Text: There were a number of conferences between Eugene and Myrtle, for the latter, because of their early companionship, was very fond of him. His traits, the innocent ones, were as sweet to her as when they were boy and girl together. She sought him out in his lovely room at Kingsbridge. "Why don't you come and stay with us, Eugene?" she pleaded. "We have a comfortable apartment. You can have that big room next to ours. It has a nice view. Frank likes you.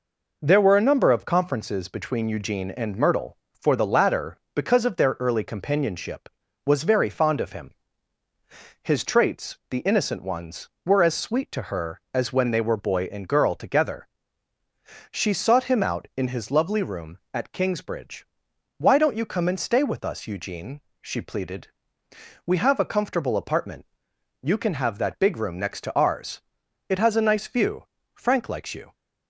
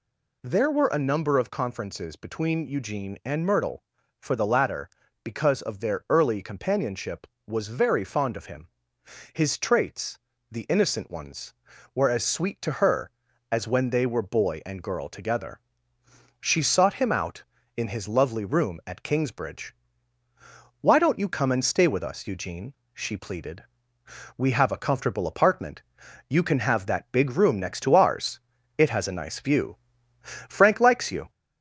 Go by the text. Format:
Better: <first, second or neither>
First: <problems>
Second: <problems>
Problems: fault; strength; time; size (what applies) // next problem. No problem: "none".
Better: first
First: none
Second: gets louder; slight; throughout; 2.5 dB